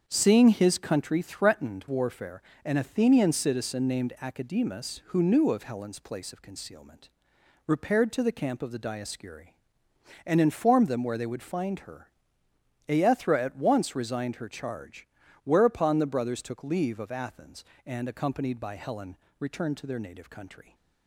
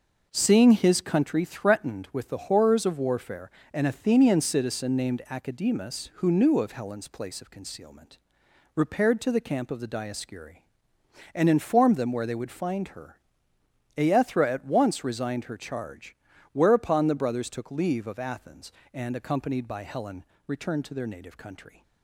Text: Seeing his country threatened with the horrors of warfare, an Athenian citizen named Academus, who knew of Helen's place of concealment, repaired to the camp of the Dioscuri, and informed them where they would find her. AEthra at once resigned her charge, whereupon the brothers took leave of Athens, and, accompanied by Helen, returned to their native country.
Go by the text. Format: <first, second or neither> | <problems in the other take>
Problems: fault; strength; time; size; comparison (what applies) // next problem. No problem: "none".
second | starts louder than the rest; strong; until 1.0 s; 7 dB // skips "with the horrors of"; at 1.8 s